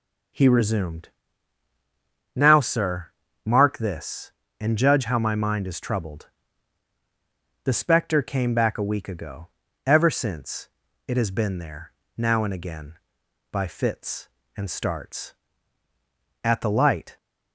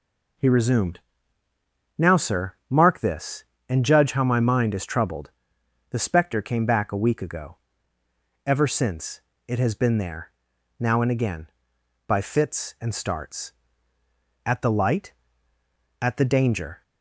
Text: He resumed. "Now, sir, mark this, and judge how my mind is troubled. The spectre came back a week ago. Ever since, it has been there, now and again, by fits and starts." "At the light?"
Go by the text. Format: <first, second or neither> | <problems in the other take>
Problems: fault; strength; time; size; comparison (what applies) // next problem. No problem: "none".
first | goes on to say "At the Danger"; noticeable; from 16.0 s on; 0.82 s long